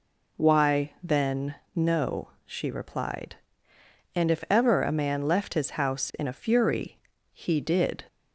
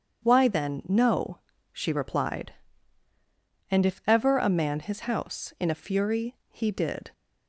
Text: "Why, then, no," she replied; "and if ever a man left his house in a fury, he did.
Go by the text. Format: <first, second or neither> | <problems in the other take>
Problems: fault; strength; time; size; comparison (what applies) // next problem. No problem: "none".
first | starts louder than the rest; strong; until 1.3 s; 8 dB // skips "left"; at 4.7 s